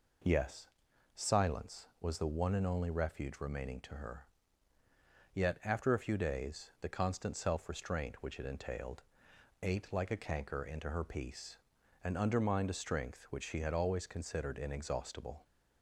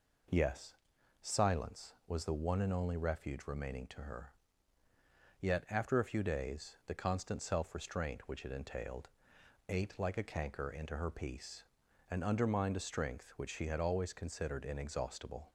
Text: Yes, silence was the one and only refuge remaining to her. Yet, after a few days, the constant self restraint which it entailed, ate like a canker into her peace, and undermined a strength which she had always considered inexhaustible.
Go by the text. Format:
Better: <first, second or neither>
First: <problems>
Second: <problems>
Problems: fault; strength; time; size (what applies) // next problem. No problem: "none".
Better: neither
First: none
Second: none